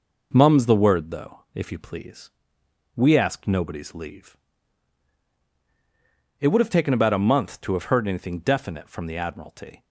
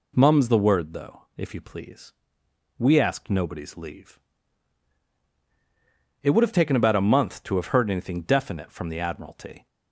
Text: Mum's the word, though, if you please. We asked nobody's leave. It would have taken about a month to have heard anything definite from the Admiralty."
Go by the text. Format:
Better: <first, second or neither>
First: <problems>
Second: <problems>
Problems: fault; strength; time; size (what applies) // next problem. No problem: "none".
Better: second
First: gets quieter; noticeable; throughout; 4.5 dB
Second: none